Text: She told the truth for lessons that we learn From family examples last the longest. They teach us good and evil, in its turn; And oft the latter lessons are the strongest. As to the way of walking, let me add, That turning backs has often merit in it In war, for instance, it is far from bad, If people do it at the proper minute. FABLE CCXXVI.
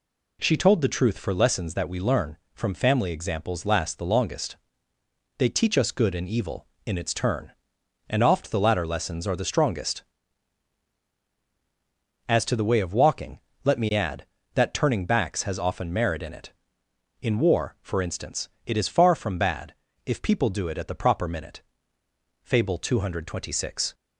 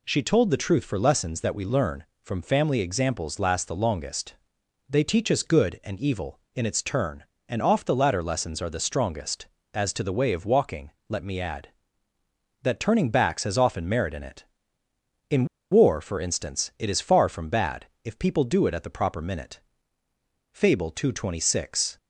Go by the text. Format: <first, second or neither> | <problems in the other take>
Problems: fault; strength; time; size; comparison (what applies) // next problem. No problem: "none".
first | pauses between "In" and "war"; slight; at 15.4 s; 0.24 s long